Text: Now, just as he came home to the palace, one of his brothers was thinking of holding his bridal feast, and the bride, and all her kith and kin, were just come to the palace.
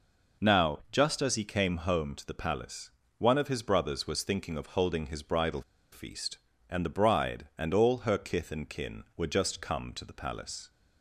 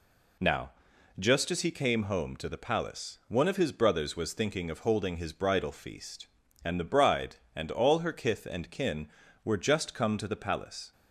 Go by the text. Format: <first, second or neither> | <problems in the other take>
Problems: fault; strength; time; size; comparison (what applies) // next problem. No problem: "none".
second | pauses between "bridal" and "feast"; slight; at 5.6 s; 0.30 s long